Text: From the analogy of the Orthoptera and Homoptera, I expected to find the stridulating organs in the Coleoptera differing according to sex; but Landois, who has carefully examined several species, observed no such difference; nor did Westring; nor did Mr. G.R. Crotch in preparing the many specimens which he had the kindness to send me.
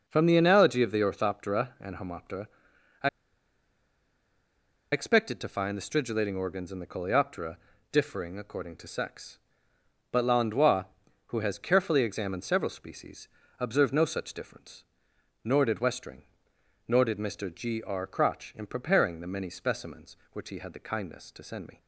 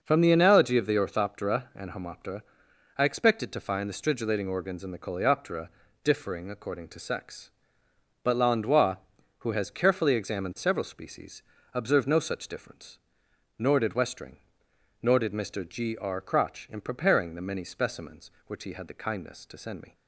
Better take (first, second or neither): second